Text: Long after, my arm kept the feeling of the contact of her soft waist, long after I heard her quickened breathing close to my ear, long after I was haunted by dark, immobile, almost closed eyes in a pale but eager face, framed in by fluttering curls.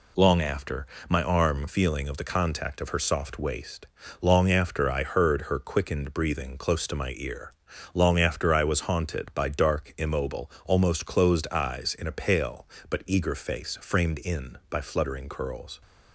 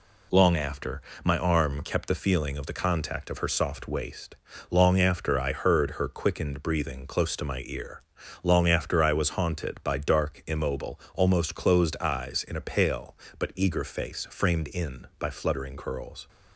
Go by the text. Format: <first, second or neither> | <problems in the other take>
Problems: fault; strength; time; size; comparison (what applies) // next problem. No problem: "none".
second | skips "kept the"; at 1.6 s